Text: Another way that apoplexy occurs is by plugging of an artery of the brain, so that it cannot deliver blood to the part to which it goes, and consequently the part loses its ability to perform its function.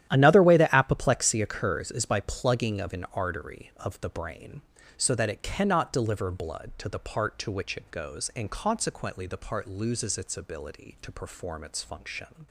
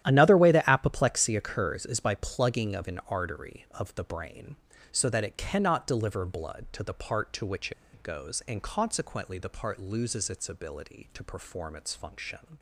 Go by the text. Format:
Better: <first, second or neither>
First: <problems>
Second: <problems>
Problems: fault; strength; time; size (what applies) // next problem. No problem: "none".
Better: first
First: starts louder than the rest; strong; until 1.1 s; 11.5 dB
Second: starts louder than the rest; strong; until 1.0 s; 11.5 dB // pauses between "which" and "it"; slight; at 7.7 s; 0.21 s long